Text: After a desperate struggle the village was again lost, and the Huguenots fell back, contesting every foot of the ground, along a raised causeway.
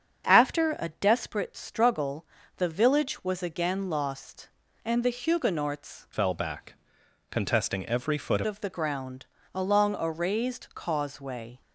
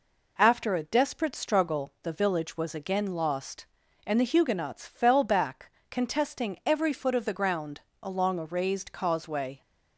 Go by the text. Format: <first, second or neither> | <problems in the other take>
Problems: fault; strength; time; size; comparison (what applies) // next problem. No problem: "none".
second | starts louder than the rest; strong; until 1.3 s; 7.5 dB // pauses between "struggle" and "the"; slight; at 2.2 s; 0.32 s long // changes voice from "fell" to "foot"; from 6.1 to 8.4 s; 2.3 s long